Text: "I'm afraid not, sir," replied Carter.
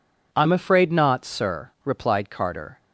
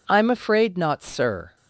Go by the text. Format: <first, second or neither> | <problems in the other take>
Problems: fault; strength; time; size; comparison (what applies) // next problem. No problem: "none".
first | stops before "replied Carter"; at 1.5 s